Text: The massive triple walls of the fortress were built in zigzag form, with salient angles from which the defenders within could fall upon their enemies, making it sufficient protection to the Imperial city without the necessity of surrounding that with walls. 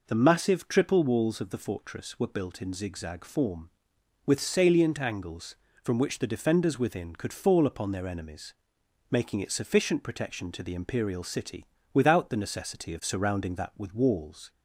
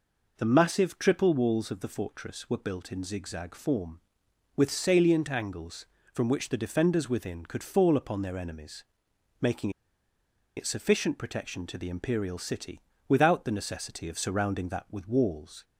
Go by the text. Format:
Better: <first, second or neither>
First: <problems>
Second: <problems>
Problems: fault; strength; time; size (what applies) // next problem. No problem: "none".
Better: first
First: pauses between "city" and "without"; slight; at 11.6 s; 0.28 s long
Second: pauses between "making" and "it"; noticeable; at 9.6 s; 0.87 s long // pauses between "city" and "without"; slight; at 12.7 s; 0.28 s long